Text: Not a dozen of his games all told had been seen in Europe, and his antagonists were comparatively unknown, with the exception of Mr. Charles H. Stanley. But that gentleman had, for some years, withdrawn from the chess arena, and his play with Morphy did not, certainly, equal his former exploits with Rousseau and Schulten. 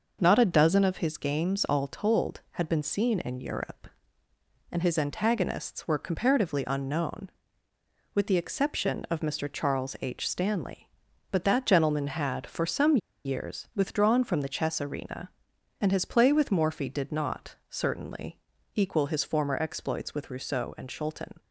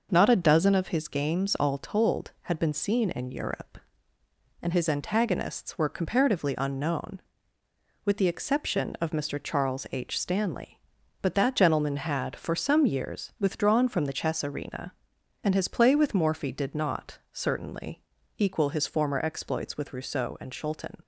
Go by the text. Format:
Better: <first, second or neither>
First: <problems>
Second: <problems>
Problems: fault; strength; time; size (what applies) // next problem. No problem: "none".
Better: second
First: pauses between "some" and "years"; slight; at 12.9 s; 0.27 s long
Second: none